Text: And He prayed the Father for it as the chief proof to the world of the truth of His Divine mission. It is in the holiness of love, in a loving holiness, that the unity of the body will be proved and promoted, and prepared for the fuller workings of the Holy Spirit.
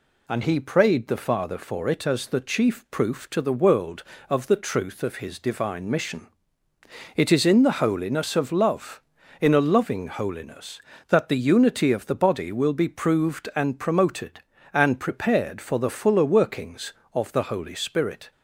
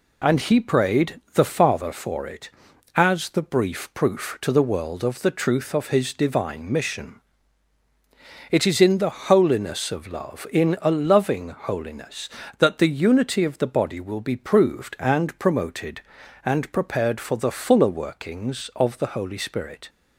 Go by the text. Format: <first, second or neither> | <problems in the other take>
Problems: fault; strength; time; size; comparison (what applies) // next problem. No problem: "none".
first | says "brief" for "chief"; at 3.4 s